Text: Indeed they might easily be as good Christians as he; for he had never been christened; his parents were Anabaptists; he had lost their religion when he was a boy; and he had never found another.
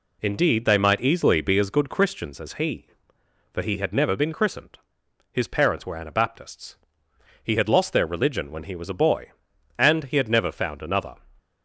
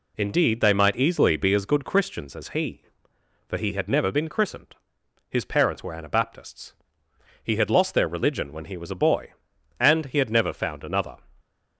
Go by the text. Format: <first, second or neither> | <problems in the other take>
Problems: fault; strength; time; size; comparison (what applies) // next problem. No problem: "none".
neither | none